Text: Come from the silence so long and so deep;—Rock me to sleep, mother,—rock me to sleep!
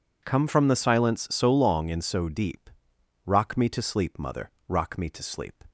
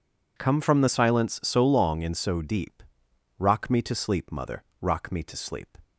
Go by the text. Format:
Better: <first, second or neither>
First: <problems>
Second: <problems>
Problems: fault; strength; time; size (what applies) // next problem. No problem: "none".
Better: neither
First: none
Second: none